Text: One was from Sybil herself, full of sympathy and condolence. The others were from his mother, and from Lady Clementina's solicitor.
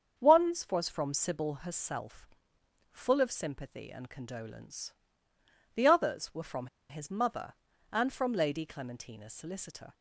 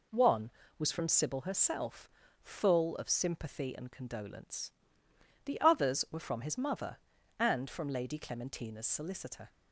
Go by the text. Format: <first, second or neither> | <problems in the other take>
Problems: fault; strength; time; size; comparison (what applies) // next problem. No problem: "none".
second | starts louder than the rest; until 1.3 s; 7 dB // pauses between "from" and "his"; slight; at 6.6 s; 0.22 s long